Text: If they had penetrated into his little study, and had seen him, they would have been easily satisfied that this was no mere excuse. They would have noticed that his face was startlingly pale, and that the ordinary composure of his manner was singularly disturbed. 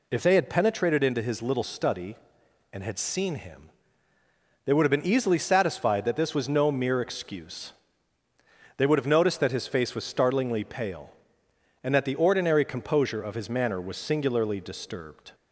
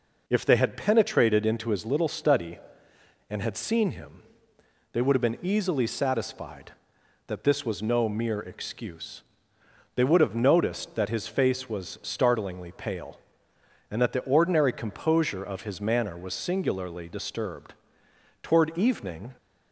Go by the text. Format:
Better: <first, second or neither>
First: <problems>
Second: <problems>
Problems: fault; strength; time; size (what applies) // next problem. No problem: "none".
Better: first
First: none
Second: goes on to say "Toward evening"; noticeable; from 18.4 s on; 0.94 s long